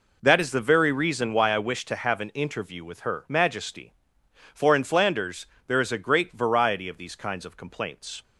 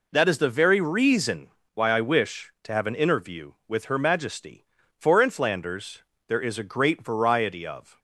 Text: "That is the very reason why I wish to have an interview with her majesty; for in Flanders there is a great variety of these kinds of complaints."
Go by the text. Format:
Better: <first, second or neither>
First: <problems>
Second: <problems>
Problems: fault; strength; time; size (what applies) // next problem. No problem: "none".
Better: first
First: pauses between "Flanders" and "there"; slight; at 5.4 s; 0.20 s long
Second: pauses between "reason" and "why"; slight; at 1.5 s; 0.24 s long // pauses between "Flanders" and "there"; slight; at 6.0 s; 0.28 s long // stops before "these kinds of complaints"; at 7.9 s